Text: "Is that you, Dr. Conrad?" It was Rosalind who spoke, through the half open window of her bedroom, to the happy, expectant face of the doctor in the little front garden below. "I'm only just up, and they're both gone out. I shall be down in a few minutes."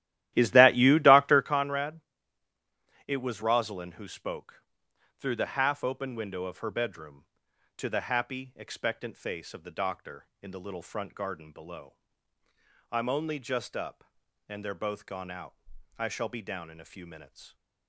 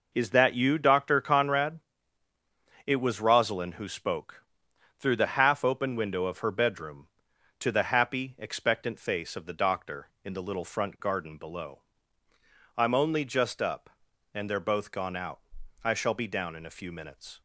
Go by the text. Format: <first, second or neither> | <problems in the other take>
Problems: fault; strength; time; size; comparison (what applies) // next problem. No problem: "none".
second | starts louder than the rest; strong; until 1.5 s; 14 dB